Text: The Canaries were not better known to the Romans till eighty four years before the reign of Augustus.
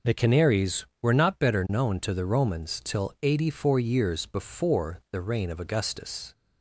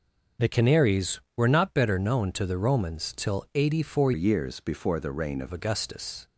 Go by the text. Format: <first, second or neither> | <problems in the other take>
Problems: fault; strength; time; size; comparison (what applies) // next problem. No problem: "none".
first | starts louder than the rest; noticeable; until 1.5 s; 6 dB // changes voice from "years" to "of"; from 4.1 to 5.5 s; 1.4 s long